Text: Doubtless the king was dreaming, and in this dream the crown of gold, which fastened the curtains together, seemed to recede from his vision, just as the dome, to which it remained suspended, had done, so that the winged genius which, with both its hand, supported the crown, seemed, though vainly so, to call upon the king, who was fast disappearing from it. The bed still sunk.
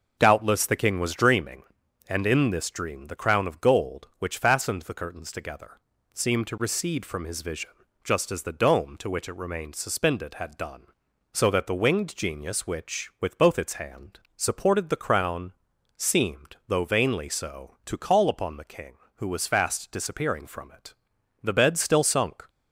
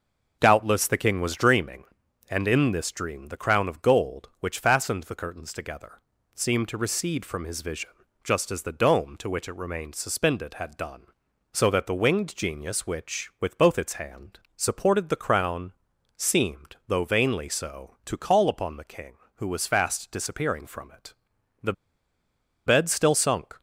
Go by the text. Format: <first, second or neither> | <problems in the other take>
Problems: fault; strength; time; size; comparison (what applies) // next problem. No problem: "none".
first | pauses between "The" and "bed"; noticeable; at 21.7 s; 0.93 s long